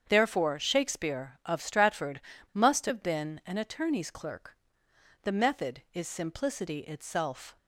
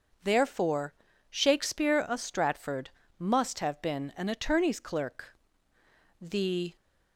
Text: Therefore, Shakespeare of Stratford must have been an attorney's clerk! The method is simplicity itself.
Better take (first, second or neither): first